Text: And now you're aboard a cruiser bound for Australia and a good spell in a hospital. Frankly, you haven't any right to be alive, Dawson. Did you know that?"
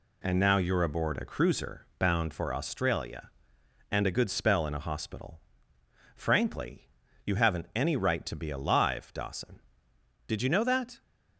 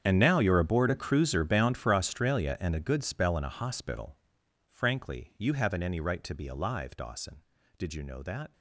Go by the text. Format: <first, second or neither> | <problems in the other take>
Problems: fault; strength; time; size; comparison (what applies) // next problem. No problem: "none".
first | gets quieter; strong; throughout; 18.5 dB